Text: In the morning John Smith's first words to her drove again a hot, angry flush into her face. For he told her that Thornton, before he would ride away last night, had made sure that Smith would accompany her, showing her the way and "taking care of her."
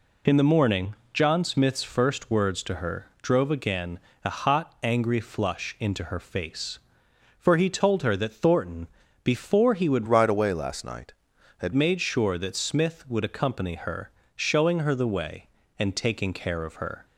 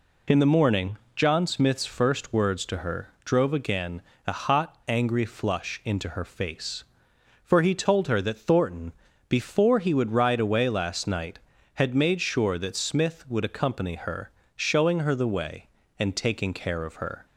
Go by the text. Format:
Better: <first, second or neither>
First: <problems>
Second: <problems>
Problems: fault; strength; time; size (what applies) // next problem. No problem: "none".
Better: second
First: pauses between "morning" and "John"; slight; at 0.9 s; 0.16 s long // pauses between "her" and "drove"; slight; at 3.0 s; 0.16 s long // pauses between "again" and "a"; slight; at 4.0 s; 0.24 s long // changes voice from "ride" to "had"; from 10.0 to 11.7 s; 1.7 s long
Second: pauses between "morning" and "John"; slight; at 0.9 s; 0.16 s long // pauses between "her" and "drove"; slight; at 3.0 s; 0.16 s long // pauses between "again" and "a"; slight; at 4.0 s; 0.24 s long